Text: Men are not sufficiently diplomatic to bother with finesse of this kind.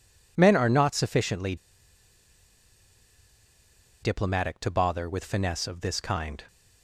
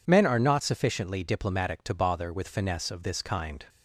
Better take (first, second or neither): second